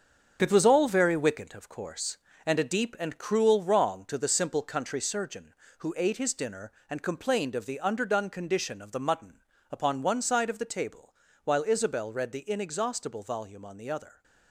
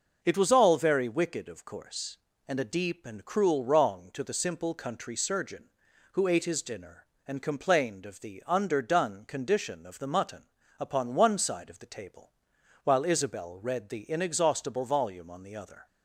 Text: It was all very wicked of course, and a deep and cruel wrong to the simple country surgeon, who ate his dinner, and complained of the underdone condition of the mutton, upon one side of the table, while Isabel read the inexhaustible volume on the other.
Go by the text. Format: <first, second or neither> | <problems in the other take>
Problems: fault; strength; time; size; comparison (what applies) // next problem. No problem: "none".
second | gets quieter; strong; throughout; 8 dB